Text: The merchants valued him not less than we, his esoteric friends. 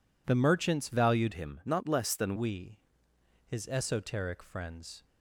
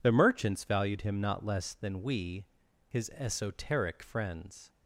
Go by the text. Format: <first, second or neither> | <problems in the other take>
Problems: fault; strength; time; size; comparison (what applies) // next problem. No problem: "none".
second | changes voice from "him" to "than"; from 1.3 to 2.3 s; 1.0 s long